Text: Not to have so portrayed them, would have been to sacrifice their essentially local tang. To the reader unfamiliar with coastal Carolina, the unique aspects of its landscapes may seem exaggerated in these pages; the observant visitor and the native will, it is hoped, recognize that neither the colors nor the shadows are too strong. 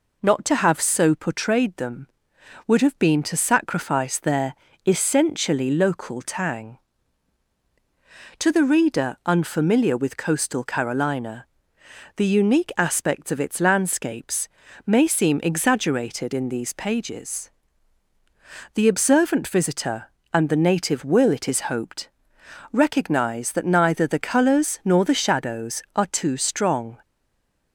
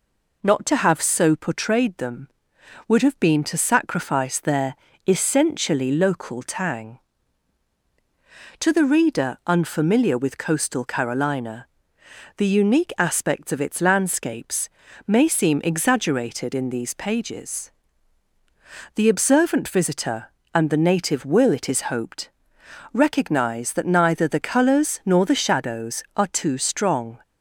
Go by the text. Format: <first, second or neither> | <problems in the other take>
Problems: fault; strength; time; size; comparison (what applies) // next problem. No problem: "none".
second | pauses between "their" and "essentially"; slight; at 4.5 s; 0.32 s long; slight in the second // pauses between "landscapes" and "may"; slight; at 14.4 s; 0.36 s long; slight in the second // stays silent after the last word; slight; from 27.0 s on; 0.7 s long